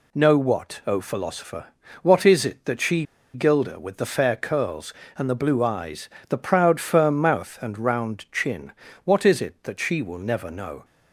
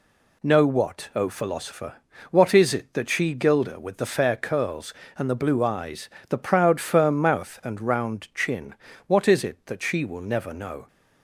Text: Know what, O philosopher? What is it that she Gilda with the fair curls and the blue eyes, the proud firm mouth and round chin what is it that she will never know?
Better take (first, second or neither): second